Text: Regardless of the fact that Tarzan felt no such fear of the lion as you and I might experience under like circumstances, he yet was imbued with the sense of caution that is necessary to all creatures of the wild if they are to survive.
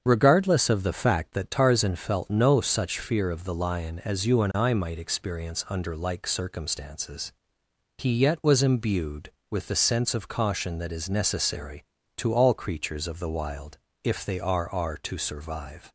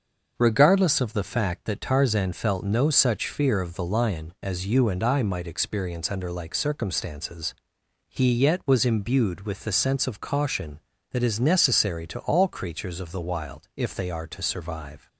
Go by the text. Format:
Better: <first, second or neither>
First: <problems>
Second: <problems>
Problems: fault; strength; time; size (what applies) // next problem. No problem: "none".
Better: second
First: starts louder than the rest; until 1.0 s; 7 dB // pauses between "wild" and "if"; slight; at 13.7 s; 0.24 s long // says "are" twice; at 14.7 s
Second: starts louder than the rest; until 1.3 s; 6.5 dB